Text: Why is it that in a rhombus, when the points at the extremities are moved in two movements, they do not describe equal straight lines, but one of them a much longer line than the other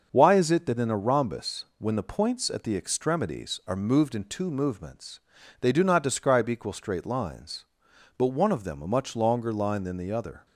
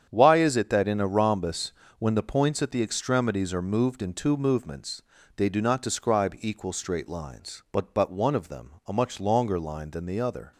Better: first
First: starts louder than the rest; until 1.1 s; 6.5 dB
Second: starts louder than the rest; strong; until 1.1 s; 8.5 dB // says "but" twice; at 7.9 s

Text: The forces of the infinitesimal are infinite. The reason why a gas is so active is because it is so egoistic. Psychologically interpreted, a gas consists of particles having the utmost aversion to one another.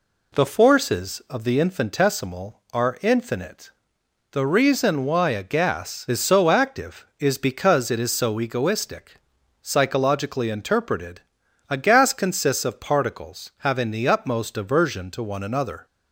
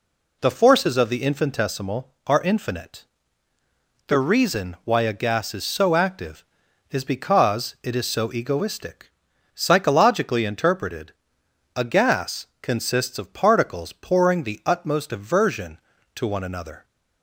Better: first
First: none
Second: pauses between "gas" and "consists"; slight; at 12.4 s; 0.16 s long // says "pouring" for "having"; at 13.9 s

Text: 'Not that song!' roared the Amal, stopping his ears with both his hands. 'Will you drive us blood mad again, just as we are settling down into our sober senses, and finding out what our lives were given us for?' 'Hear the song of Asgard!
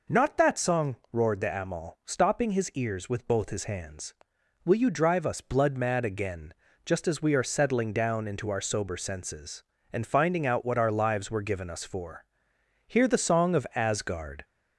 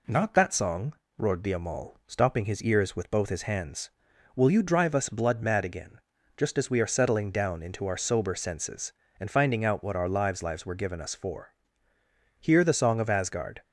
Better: first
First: none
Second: says "lives" twice; at 10.4 s

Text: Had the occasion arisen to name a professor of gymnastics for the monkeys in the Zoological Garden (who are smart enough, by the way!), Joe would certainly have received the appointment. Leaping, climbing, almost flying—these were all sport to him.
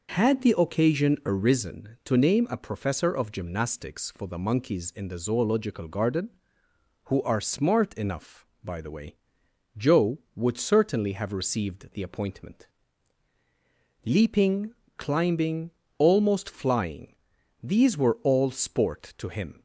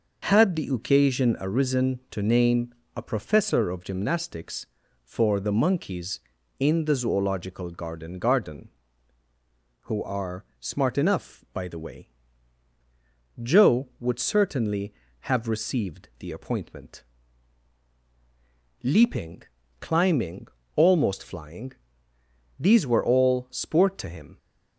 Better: first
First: none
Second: pauses between "name" and "a"; slight; at 2.7 s; 0.22 s long // says "Garden" twice; at 8.1 s // pauses between "are" and "smart"; slight; at 10.4 s; 0.16 s long

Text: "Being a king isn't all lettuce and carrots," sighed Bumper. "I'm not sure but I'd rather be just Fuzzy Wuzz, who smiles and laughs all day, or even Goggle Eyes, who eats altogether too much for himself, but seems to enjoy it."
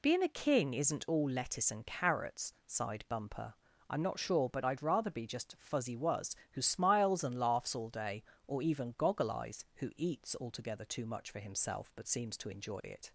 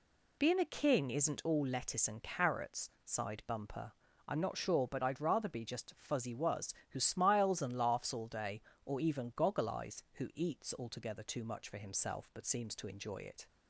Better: neither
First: none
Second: none

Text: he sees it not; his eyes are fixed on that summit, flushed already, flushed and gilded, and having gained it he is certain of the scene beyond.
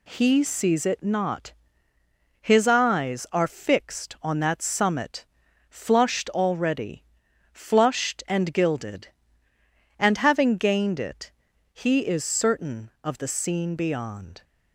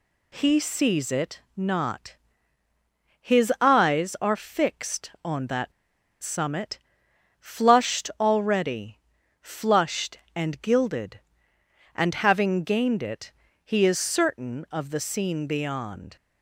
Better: first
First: pauses between "it" and "he"; at 11.3 s; 0.40 s long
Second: pauses between "that" and "summit"; noticeable; at 5.7 s; 0.51 s long // pauses between "it" and "he"; slight; at 13.3 s; 0.32 s long

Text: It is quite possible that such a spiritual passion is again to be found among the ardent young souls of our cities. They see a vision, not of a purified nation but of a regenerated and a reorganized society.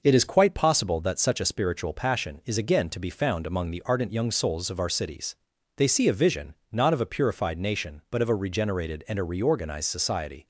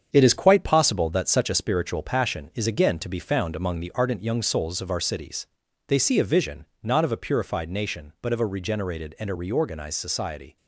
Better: first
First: none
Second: gets quieter; throughout; 6.5 dB

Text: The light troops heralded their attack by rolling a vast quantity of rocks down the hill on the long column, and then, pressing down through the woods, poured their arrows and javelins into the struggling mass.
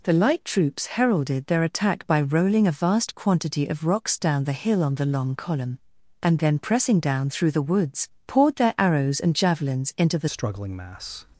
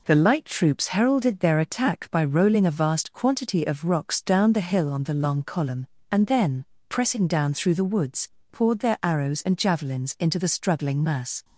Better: second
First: changes voice at "struggling"; from 10.2 s on; 1.0 s long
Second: none

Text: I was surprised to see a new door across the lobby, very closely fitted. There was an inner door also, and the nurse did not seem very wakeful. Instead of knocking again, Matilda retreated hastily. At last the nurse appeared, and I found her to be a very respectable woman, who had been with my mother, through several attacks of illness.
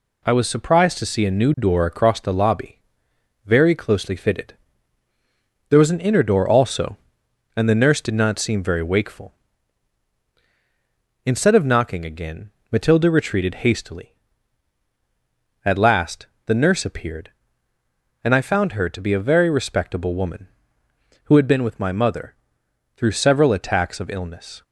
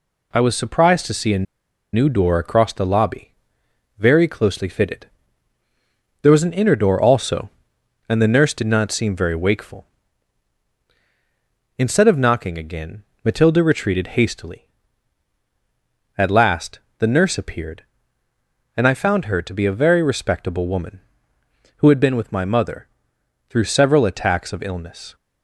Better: first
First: pauses between "last" and "the"; slight; at 16.2 s; 0.18 s long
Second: pauses between "a" and "new"; noticeable; at 1.4 s; 0.50 s long // pauses between "last" and "the"; slight; at 16.7 s; 0.18 s long

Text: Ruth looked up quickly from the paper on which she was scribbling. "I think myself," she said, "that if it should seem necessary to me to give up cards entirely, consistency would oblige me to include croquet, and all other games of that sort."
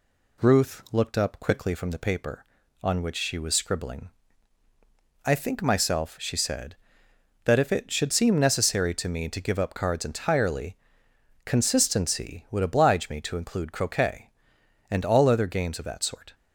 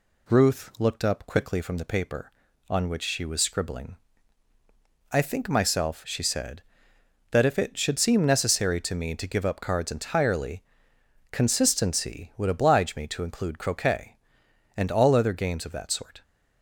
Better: neither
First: none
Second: none

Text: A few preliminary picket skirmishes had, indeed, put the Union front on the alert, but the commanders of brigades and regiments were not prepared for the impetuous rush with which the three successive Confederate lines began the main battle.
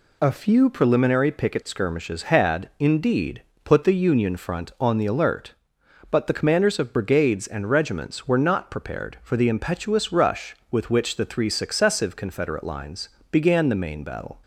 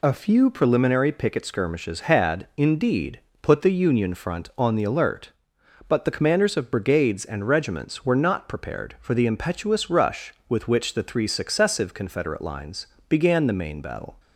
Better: neither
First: pauses between "lines" and "began"; slight; at 13.0 s; 0.20 s long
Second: pauses between "lines" and "began"; slight; at 12.8 s; 0.20 s long

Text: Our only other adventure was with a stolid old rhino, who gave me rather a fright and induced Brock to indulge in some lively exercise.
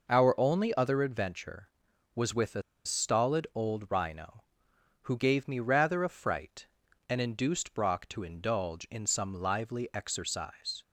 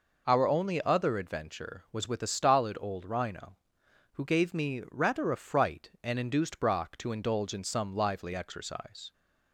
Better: second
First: pauses between "a" and "stolid"; slight; at 2.6 s; 0.24 s long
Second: none

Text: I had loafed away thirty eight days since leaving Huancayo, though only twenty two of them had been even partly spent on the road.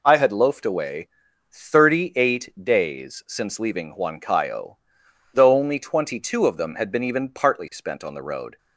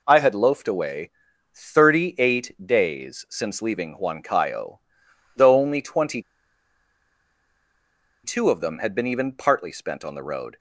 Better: first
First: pauses between "away" and "thirty"; at 1.0 s; 0.44 s long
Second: pauses between "away" and "thirty"; at 1.1 s; 0.44 s long // pauses between "twenty" and "two"; strong; at 6.2 s; 2.0 s long

